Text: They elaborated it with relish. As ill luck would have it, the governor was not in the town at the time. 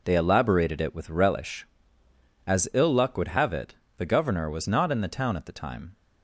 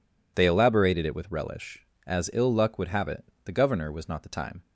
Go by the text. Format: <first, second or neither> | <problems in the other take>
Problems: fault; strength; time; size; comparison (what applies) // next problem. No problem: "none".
first | skips "in the town at"; at 4.2 s